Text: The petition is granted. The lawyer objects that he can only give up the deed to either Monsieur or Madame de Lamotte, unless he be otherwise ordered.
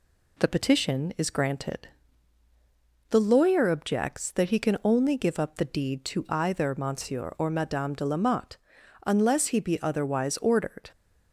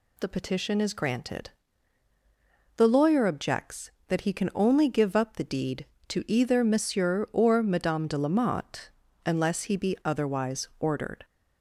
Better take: neither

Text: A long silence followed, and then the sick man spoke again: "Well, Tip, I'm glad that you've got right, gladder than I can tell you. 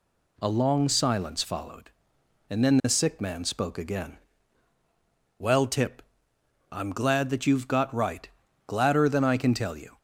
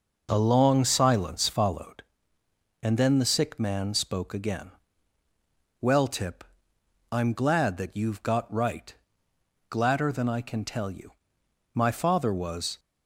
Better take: first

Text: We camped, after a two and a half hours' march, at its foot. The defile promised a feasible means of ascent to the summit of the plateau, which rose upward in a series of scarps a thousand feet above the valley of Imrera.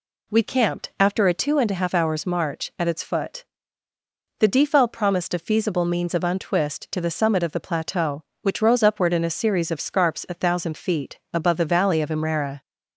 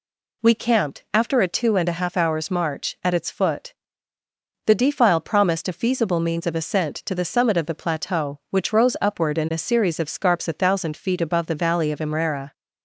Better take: second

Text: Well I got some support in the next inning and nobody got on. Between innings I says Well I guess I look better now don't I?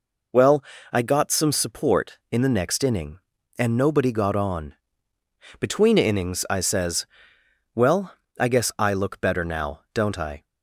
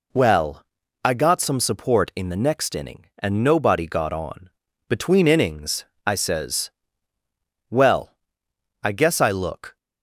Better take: first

